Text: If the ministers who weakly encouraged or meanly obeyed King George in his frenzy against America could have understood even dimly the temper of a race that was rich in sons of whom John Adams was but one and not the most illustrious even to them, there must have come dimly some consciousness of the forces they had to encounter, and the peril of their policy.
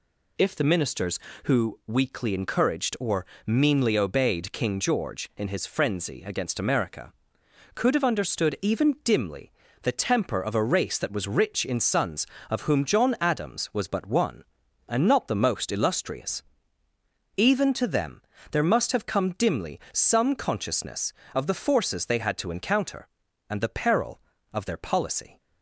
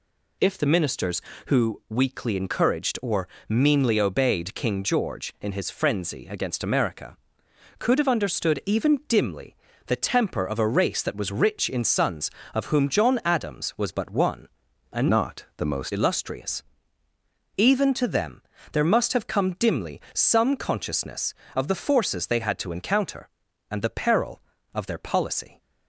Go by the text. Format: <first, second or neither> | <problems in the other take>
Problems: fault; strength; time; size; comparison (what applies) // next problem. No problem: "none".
first | pauses between "or" and "meanly"; slight; at 3.2 s; 0.20 s long; slight in the first // pauses between "dimly" and "the"; slight; at 9.5 s; 0.32 s long; slight in the first // changes voice from "not" to "most"; from 15.1 to 15.9 s; 0.8 s long // pauses between "illustrious" and "even"; noticeable; at 16.6 s; 0.94 s long; noticeable in the first